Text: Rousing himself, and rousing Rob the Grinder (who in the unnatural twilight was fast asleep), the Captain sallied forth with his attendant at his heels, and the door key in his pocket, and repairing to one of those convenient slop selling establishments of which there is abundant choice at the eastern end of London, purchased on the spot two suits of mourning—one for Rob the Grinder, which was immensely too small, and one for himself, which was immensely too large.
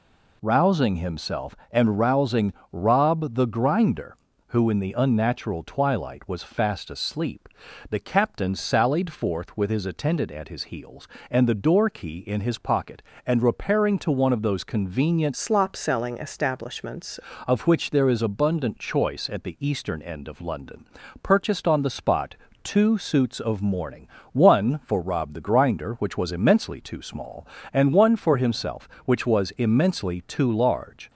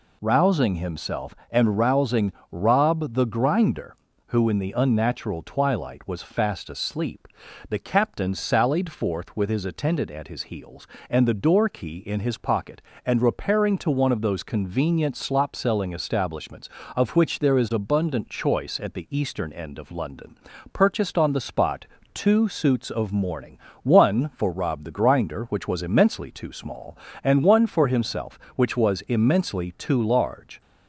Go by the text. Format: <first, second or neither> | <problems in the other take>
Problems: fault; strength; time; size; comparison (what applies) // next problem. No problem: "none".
second | pauses between "rousing" and "Rob"; slight; at 2.5 s; 0.18 s long; slight in the second // changes voice from "slop" to "establishments"; from 15.3 to 17.1 s; 1.8 s long // pauses between "spot" and "two"; slight; at 22.3 s; 0.28 s long; slight in the second